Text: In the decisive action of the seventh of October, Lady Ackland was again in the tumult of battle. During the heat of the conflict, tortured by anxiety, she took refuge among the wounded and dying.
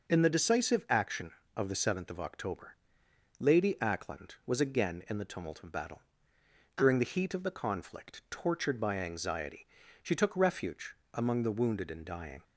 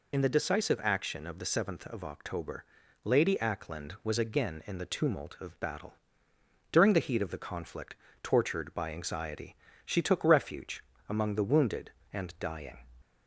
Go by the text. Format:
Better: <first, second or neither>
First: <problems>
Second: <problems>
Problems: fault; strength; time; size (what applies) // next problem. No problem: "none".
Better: first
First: pauses between "refuge" and "among"; slight; at 10.9 s; 0.16 s long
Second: loses the start of "In"; at 0.1 s; 45 ms // pauses between "refuge" and "among"; slight; at 10.8 s; 0.26 s long